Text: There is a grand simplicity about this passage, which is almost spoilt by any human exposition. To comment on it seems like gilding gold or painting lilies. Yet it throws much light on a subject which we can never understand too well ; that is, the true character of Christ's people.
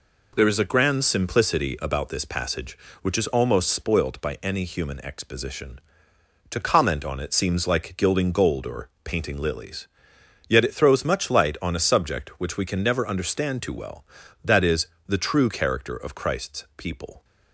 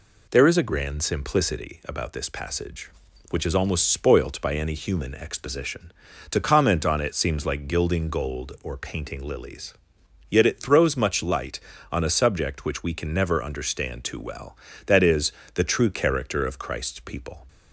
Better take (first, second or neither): neither